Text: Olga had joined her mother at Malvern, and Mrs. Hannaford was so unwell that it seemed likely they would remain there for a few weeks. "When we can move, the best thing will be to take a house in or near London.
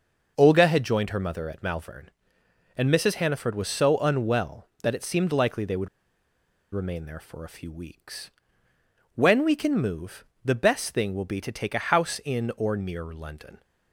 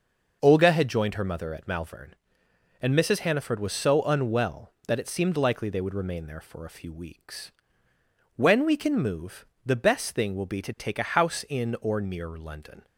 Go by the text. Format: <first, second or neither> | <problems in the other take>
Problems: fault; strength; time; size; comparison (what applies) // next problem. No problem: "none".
second | pauses between "would" and "remain"; noticeable; at 5.8 s; 0.86 s long